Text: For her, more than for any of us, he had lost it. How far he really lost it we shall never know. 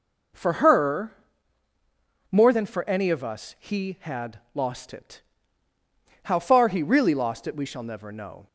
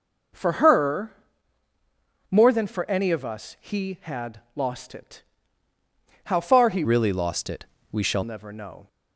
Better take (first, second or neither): first